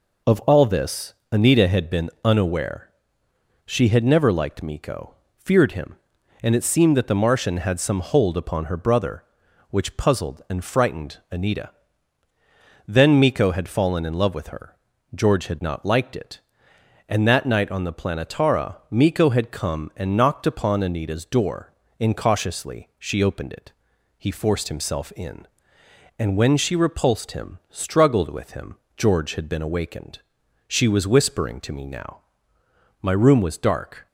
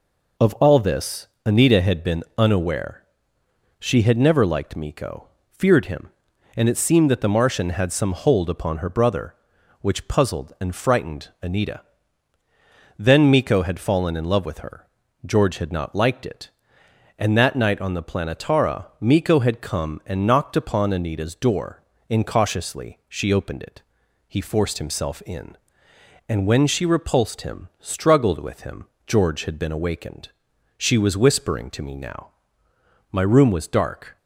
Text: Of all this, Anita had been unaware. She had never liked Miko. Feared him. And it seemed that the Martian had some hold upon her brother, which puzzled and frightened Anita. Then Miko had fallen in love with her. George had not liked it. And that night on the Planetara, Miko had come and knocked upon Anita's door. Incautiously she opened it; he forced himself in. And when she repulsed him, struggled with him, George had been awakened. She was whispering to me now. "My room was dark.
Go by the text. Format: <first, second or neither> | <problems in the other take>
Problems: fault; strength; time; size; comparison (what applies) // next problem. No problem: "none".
neither | none